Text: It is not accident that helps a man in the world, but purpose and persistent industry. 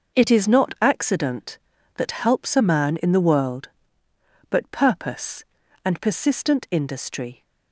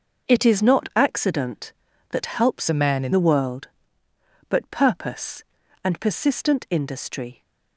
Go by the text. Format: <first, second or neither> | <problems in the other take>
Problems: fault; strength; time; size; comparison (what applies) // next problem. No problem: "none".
first | changes voice from "a" to "in"; from 2.6 to 3.1 s; 0.5 s long